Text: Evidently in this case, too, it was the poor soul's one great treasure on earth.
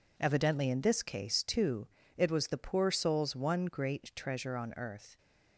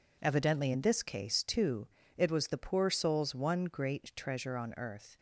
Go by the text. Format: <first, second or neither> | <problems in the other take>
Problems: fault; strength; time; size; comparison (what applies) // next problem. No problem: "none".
neither | none